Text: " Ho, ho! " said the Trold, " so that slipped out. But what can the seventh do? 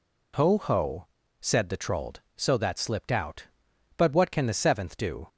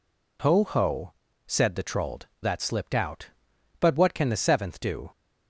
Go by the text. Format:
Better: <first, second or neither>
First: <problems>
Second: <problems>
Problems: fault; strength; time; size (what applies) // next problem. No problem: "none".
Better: first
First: none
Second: skips "so"; at 2.4 s